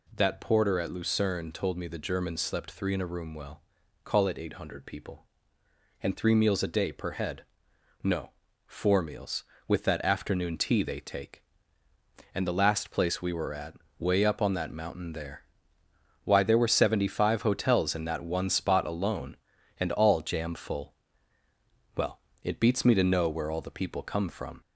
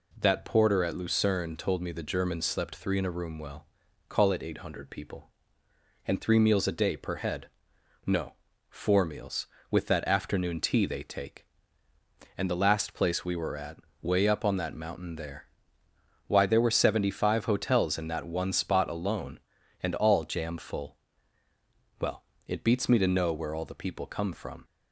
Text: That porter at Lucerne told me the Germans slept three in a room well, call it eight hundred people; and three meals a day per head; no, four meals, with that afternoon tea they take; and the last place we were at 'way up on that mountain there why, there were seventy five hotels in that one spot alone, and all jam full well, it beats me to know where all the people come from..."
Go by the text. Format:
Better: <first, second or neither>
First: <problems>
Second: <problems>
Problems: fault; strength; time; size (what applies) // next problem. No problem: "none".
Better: second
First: gets louder; slight; throughout; 2.5 dB // pauses between "at" and "way"; slight; at 13.7 s; 0.24 s long // pauses between "there" and "why"; noticeable; at 15.4 s; 0.82 s long // pauses between "full" and "well"; at 20.9 s; 1.0 s long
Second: pauses between "at" and "way"; slight; at 13.7 s; 0.24 s long // pauses between "there" and "why"; noticeable; at 15.4 s; 0.82 s long // pauses between "full" and "well"; at 20.9 s; 1.0 s long